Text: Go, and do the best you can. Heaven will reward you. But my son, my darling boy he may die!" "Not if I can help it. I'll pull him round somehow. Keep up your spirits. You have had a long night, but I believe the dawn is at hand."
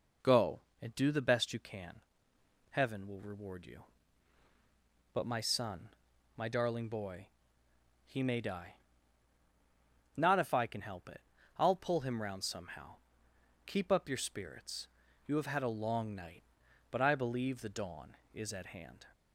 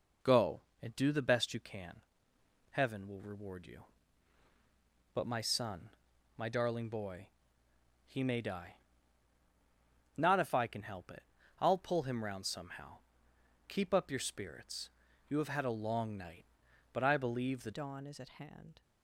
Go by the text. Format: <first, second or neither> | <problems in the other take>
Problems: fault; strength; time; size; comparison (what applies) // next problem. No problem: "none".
first | pauses between "boy" and "he"; noticeable; at 7.2 s; 0.76 s long; noticeable in the first // changes voice at "dawn"; from 17.7 s on; 1.1 s long